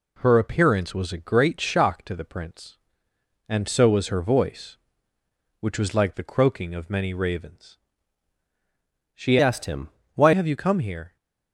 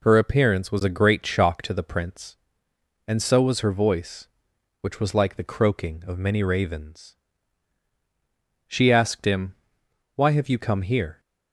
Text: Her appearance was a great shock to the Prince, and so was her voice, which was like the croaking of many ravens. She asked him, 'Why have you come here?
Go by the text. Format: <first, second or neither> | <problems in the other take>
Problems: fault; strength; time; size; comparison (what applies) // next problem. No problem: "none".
second | changes voice from "asked" to "Why"; from 9.4 to 10.3 s; 0.9 s long